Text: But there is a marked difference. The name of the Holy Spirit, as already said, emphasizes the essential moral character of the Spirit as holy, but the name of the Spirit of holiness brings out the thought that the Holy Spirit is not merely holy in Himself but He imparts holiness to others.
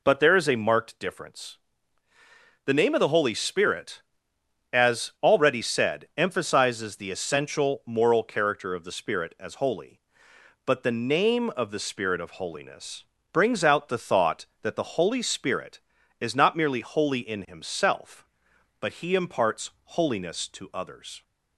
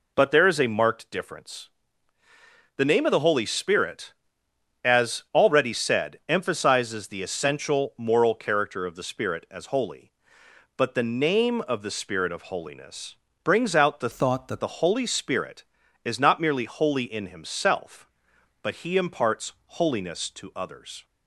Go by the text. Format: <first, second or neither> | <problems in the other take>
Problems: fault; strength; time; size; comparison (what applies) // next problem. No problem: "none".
first | pauses between "holiness" and "brings"; slight; at 13.1 s; 0.28 s long; slight in the first // changes voice from "thought" to "that"; from 14.1 to 14.6 s; 0.5 s long // pauses between "imparts" and "holiness"; slight; at 19.5 s; 0.16 s long; slight in the first